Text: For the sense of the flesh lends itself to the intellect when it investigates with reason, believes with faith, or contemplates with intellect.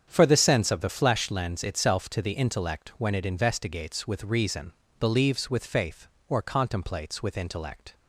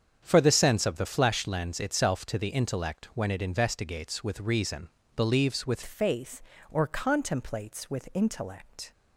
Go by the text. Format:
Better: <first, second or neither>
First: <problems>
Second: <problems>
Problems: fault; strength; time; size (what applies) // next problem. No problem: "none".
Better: first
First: starts louder than the rest; strong; until 1.0 s; 8 dB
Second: starts louder than the rest; strong; until 1.2 s; 8 dB // changes voice at "faith"; from 5.8 s on; 3.1 s long